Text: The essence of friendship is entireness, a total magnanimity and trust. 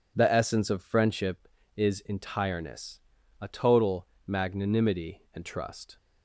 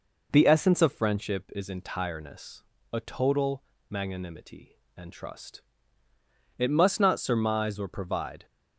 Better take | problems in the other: first | pauses between "total" and "magnanimity"; slight; at 3.6 s; 0.26 s long; slight in the first // goes on to say "It must not surmise or provide"; strong; from 6.5 s on; 1.8 s long

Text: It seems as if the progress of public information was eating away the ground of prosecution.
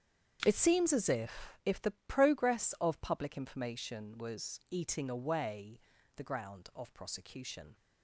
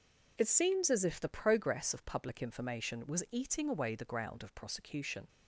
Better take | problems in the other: second | starts louder than the rest; strong; until 1.4 s; 8 dB // says "if" twice; at 1.6 s // pauses between "away" and "the"; slight; at 5.7 s; 0.36 s long

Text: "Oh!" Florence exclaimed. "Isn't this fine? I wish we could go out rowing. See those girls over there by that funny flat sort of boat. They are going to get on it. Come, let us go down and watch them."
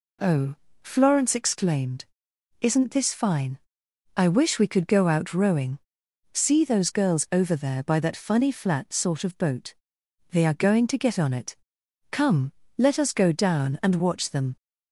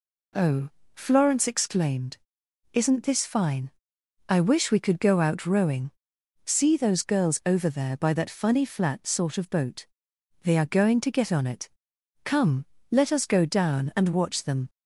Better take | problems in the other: neither | none

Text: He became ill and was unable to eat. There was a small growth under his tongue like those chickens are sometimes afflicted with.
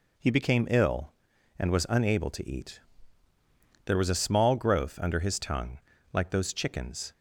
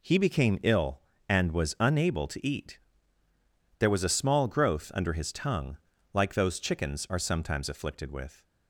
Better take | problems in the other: second | pauses between "tongue" and "like"; slight; at 5.7 s; 0.34 s long; slight in the second // stops before "are sometimes afflicted with"; at 7.1 s

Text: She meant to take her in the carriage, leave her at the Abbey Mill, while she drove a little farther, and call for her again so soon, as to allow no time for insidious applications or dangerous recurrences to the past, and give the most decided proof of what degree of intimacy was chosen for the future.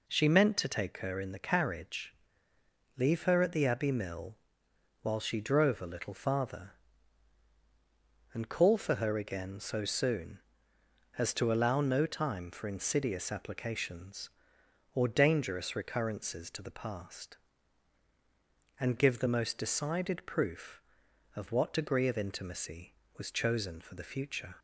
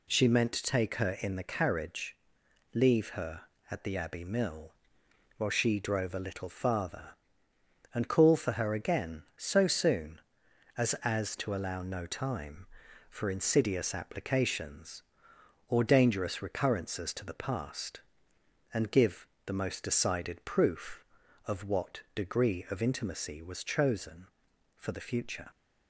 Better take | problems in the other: first | says "as" twice; at 11.0 s // pauses between "give" and "the"; slight; at 19.2 s; 0.18 s long

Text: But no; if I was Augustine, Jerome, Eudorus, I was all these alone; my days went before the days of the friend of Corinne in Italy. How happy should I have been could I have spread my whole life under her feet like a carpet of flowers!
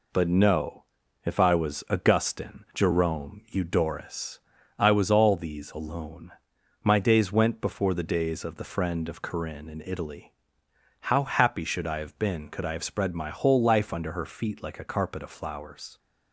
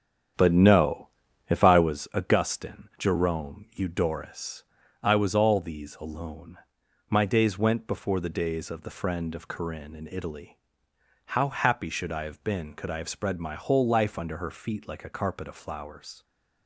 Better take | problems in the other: first | starts louder than the rest; strong; until 1.9 s; 8.5 dB

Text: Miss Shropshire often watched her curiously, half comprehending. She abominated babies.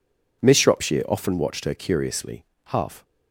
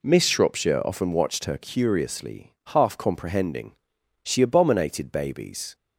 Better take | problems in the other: second | stops before "comprehending She abominated babies"; at 3.0 s

